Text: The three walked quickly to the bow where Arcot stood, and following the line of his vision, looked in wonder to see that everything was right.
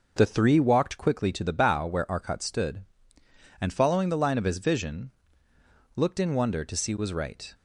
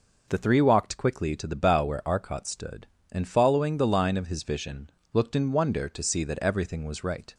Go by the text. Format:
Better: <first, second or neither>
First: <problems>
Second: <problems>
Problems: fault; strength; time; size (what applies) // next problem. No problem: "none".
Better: second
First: skips "that everything"; at 6.9 s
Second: none